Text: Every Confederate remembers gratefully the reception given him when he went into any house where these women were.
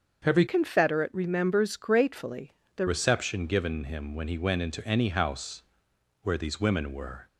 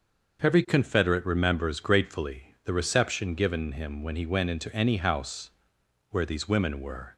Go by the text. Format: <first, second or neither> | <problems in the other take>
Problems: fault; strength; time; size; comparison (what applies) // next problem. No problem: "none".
second | starts louder than the rest; until 1.2 s; 6.5 dB; also in the second // changes voice from "Confederate" to "the"; from 0.4 to 2.8 s; 2.4 s long // pauses between "gratefully" and "the"; slight; at 2.5 s; 0.26 s long // pauses between "house" and "where"; noticeable; at 5.6 s; 0.60 s long; noticeable in the second